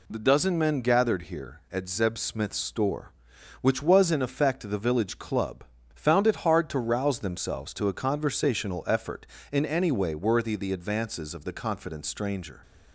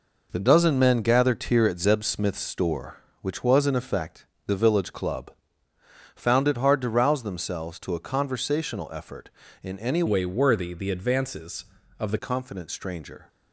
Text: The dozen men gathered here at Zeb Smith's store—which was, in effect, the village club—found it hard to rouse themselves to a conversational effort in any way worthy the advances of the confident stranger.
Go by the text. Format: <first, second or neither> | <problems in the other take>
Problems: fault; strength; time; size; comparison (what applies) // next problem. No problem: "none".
first | changes voice from "way" to "the"; from 10.0 to 12.1 s; 2.1 s long